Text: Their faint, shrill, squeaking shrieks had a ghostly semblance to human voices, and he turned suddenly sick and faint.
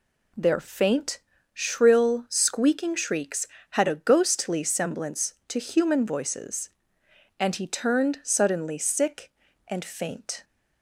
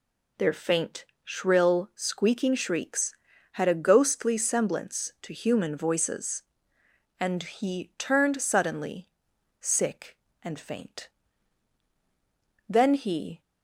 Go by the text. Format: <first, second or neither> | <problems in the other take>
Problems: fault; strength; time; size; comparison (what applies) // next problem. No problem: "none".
first | pauses between "suddenly" and "sick"; noticeable; at 9.1 s; 0.49 s long // goes on to say "Then he"; noticeable; from 12.6 s on; 0.72 s long